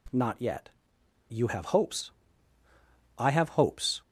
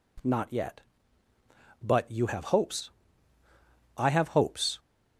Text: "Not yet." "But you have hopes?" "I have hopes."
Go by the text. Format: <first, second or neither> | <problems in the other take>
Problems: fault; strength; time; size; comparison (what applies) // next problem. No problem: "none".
second | skips "But"; at 1.0 s